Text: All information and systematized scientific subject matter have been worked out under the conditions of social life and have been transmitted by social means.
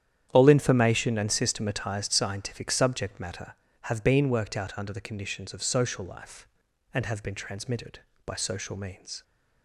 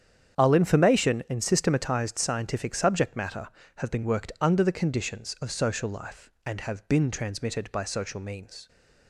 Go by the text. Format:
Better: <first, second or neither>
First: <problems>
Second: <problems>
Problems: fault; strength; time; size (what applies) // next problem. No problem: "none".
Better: first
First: starts louder than the rest; strong; until 1.3 s; 10 dB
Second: starts louder than the rest; strong; until 1.4 s; 8.5 dB // skips "out"; at 4.3 s